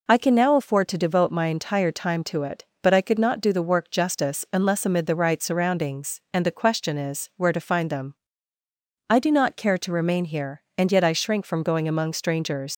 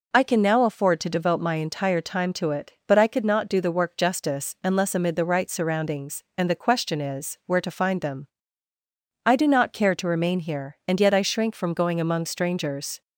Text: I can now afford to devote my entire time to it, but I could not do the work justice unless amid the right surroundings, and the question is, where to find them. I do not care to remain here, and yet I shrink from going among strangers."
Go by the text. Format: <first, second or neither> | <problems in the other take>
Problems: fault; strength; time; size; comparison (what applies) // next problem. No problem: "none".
second | leaves "strangers" unfinished; at 12.7 s; 130 ms